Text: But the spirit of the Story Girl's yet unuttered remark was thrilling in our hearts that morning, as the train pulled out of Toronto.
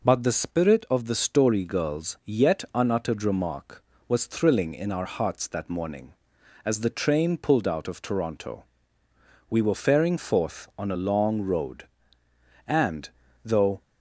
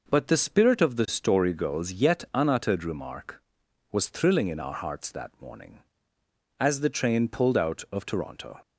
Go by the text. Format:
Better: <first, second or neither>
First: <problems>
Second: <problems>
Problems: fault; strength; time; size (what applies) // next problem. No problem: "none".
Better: second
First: goes on to say "We were faring forth on a long road and though"; strong; from 9.4 s on; 4.3 s long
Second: none